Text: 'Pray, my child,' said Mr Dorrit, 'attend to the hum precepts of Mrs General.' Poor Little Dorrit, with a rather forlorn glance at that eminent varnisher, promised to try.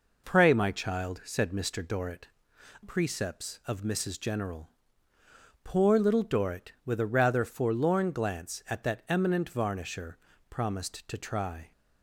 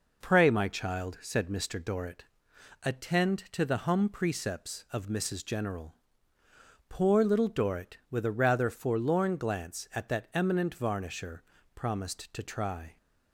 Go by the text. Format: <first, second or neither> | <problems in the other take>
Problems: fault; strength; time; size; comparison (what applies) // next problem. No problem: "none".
second | skips "attend to the hum"; at 2.5 s